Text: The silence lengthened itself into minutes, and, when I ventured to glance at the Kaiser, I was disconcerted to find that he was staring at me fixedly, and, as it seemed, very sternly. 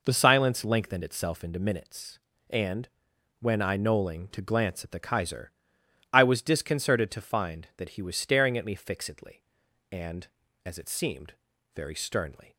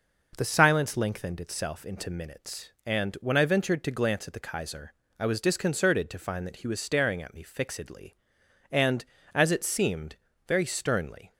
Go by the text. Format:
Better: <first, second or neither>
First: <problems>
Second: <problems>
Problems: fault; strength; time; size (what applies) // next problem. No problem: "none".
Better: second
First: says "knolling" for "ventured"; at 3.7 s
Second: none